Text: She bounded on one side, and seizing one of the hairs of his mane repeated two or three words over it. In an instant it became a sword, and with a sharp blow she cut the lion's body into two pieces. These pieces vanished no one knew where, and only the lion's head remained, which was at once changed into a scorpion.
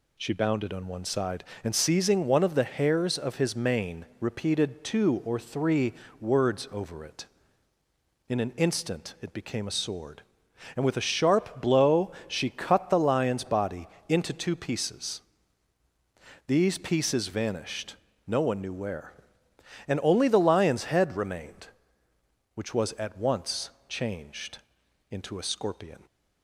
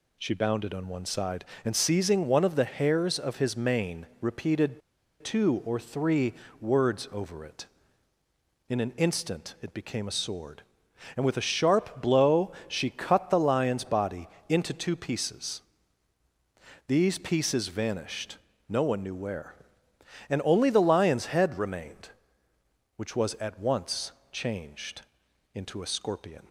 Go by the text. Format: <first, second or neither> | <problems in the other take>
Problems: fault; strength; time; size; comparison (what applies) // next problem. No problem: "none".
first | pauses between "repeated" and "two"; at 4.8 s; 0.42 s long // pauses between "three" and "words"; slight; at 6.3 s; 0.28 s long; slight in the first // pauses between "blow" and "she"; slight; at 12.5 s; 0.16 s long; slight in the first // pauses between "body" and "into"; slight; at 14.2 s; 0.22 s long; slight in the first // pauses between "vanished" and "no"; slight; at 18.3 s; 0.34 s long; slight in the first // pauses between "once" and "changed"; slight; at 24.1 s; 0.22 s long; slight in the first // pauses between "changed" and "into"; noticeable; at 25.0 s; 0.52 s long; noticeable in the first